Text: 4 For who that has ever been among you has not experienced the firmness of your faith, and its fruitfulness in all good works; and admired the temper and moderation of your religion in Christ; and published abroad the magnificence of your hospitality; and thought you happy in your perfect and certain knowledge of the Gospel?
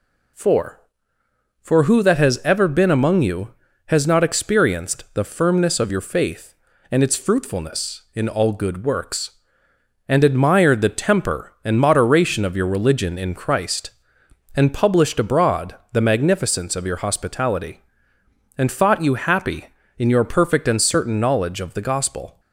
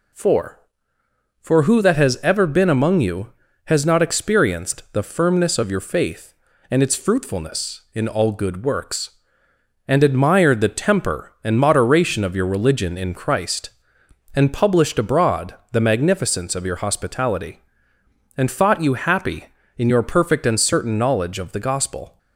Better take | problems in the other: neither | pauses between "abroad" and "the"; slight; the same in both

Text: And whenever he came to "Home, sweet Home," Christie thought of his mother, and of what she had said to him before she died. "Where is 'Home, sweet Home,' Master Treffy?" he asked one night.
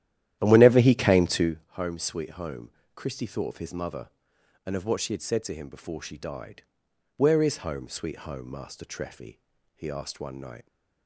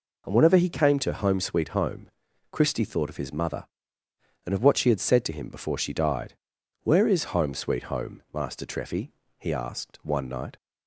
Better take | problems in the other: second | starts louder than the rest; strong; until 1.5 s; 12 dB

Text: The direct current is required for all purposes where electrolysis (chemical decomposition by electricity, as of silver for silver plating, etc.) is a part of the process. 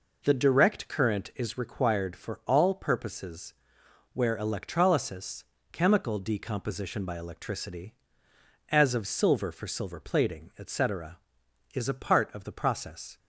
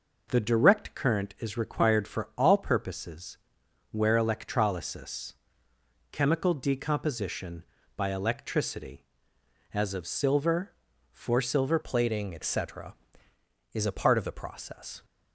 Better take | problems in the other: first | pauses between "purposes" and "where"; noticeable; at 3.3 s; 0.52 s long; noticeable in the first // changes voice at "plating"; from 11.8 s on; 3.2 s long

